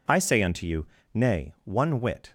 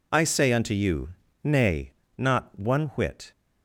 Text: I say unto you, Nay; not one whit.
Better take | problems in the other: second | skips "not"; at 1.5 s

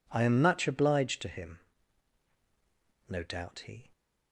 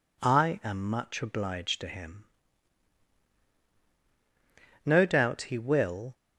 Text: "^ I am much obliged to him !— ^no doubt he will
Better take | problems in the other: second | stops before "will"; at 3.9 s

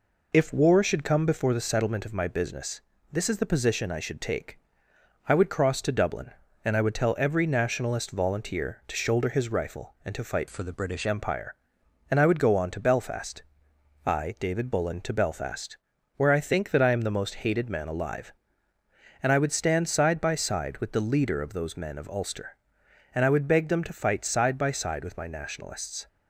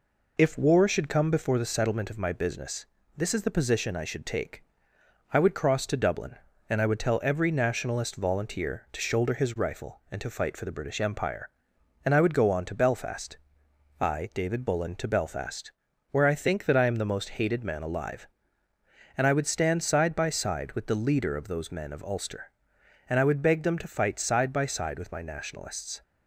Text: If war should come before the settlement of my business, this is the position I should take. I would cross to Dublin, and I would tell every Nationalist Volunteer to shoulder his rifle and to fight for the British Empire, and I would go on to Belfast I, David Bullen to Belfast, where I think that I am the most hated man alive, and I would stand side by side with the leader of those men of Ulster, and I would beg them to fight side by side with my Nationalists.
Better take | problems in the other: second | changes voice from "for" to "British"; from 10.4 to 11.0 s; 0.6 s long // pauses between "Belfast" and "I"; noticeable; at 13.4 s; 0.64 s long; noticeable in the second

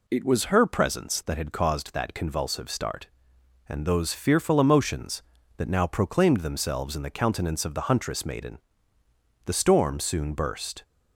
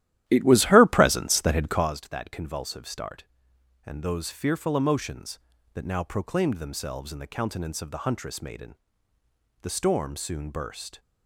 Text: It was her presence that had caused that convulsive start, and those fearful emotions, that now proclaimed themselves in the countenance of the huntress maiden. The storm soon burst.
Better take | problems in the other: first | starts louder than the rest; strong; until 1.9 s; 13 dB

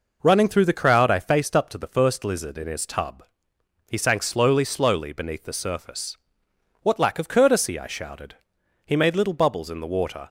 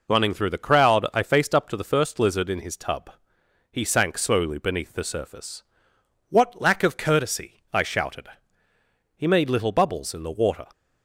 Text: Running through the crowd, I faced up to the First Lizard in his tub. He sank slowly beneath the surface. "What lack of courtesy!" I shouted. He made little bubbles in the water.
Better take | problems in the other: second | says "slowly" twice; at 4.6 s

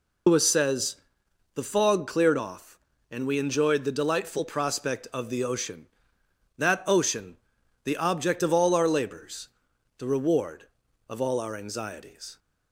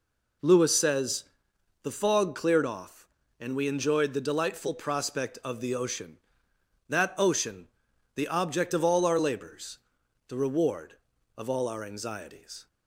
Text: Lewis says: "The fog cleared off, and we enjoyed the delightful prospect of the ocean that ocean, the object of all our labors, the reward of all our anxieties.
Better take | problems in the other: second | loses the start of "Lewis"; at 0.2 s; 130 ms

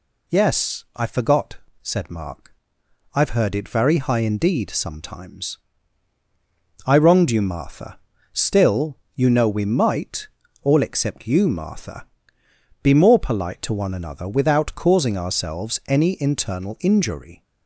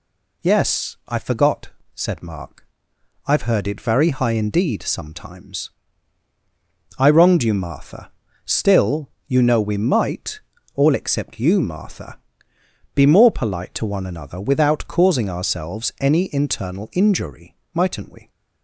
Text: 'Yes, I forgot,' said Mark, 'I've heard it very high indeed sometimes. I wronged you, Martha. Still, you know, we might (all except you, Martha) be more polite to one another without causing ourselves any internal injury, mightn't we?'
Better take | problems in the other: second | stops before "mightn't we"; at 17.4 s

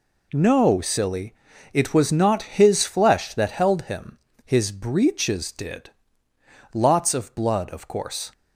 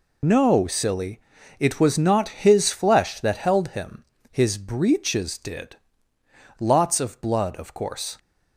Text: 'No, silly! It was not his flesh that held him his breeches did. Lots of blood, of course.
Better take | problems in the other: first | loses the start of "No"; at 0.2 s; 60 ms // pauses between "him" and "his"; slight; at 4.0 s; 0.26 s long; slight in the first

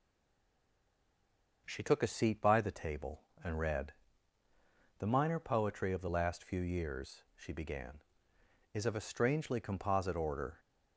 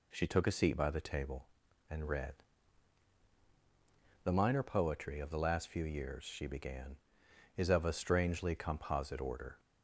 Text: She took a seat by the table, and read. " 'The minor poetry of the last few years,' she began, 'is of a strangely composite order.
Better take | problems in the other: second | stays silent before the first word; noticeable; until 1.6 s; 1.6 s long

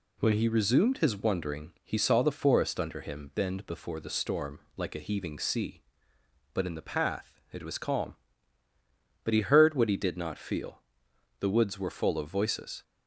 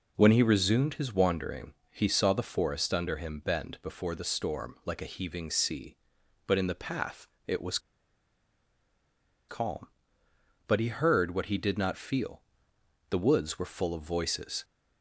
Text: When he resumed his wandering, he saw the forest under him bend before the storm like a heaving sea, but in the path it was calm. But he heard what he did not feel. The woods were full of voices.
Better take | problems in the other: first | pauses between "path" and "it"; slight; at 7.2 s; 0.18 s long // pauses between "was" and "calm"; strong; at 7.7 s; 1.7 s long

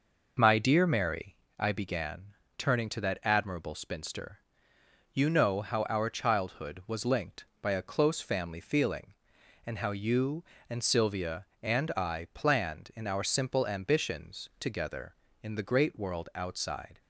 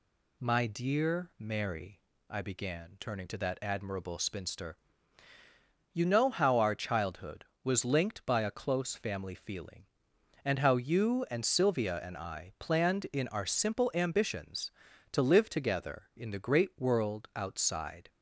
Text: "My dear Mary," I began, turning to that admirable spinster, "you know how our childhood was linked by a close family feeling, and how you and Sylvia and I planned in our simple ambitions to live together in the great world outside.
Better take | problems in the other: second | skips "to live"; at 14.5 s

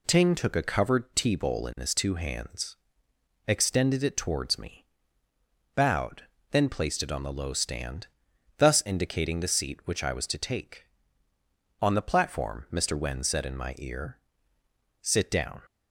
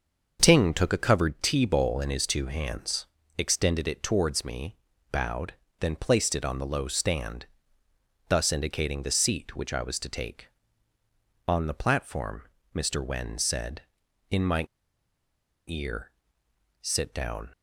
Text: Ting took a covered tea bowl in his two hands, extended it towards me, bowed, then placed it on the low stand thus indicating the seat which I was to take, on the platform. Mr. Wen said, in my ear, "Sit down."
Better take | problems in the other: first | starts louder than the rest; until 1.4 s; 6.5 dB // pauses between "stand" and "thus"; noticeable; at 7.4 s; 0.82 s long; noticeable in the first // pauses between "my" and "ear"; at 14.6 s; 1.0 s long

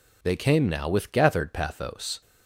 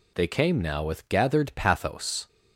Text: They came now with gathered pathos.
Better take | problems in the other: neither | none

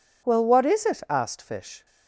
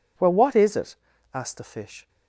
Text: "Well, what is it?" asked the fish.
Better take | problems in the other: second | skips "the"; at 1.4 s

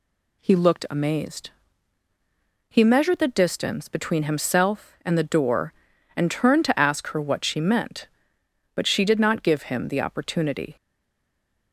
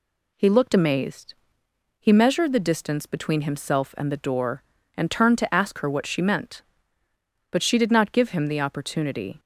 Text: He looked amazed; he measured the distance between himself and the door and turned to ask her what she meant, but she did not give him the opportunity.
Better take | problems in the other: second | stays silent after the last word; from 10.7 s on; 1.0 s long

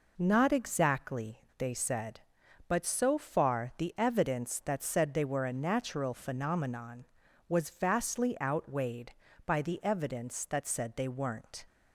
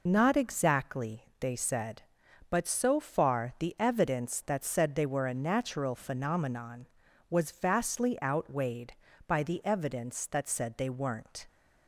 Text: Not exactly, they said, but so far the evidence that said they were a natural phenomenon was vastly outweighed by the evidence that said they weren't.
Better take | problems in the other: first | loses the start of "Not"; at 0.0 s; 35 ms

